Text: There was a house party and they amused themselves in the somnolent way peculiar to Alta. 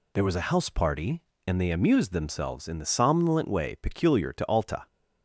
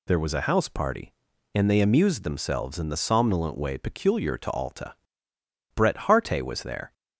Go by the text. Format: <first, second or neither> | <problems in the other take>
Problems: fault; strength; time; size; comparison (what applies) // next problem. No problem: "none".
first | goes on to say "Bret Harte was there"; noticeable; from 5.7 s on; 1.1 s long